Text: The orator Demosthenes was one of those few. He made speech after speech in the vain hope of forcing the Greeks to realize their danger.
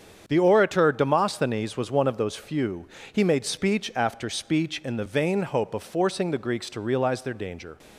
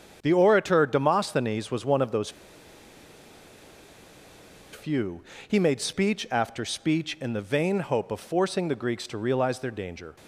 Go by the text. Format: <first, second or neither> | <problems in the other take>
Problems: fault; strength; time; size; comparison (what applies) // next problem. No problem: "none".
first | starts louder than the rest; strong; until 1.2 s; 8 dB; strong in the first // pauses between "those" and "few"; strong; at 2.2 s; 2.4 s long